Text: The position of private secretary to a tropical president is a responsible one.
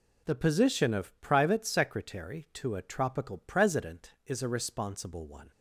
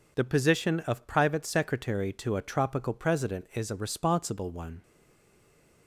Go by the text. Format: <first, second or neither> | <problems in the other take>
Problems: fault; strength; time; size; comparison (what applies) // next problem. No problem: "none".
first | stays silent after the last word; from 4.8 s on; 1.0 s long